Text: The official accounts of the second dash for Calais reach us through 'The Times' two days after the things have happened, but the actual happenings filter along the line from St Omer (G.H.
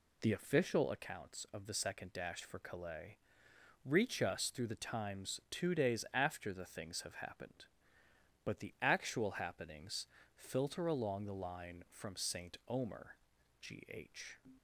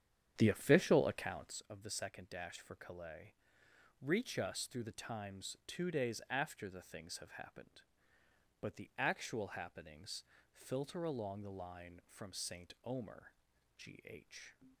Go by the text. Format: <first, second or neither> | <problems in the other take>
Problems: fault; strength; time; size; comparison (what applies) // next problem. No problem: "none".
first | starts louder than the rest; strong; until 1.7 s; 8.5 dB // pauses between "Calais" and "reach"; noticeable; at 3.3 s; 0.66 s long; noticeable in the first // pauses between "happenings" and "filter"; slight; at 10.2 s; 0.28 s long; slight in the first